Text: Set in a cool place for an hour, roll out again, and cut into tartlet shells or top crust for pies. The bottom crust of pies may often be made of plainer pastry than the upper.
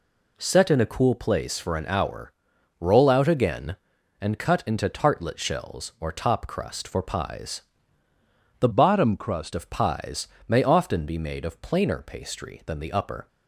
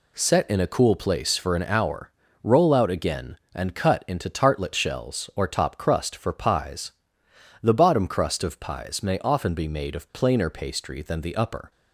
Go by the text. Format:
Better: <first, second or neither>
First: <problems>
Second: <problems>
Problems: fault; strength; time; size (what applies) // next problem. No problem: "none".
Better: second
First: changes voice from "bottom" to "crust"; from 8.7 to 9.5 s; 0.8 s long // pauses between "pies" and "may"; slight; at 10.2 s; 0.20 s long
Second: none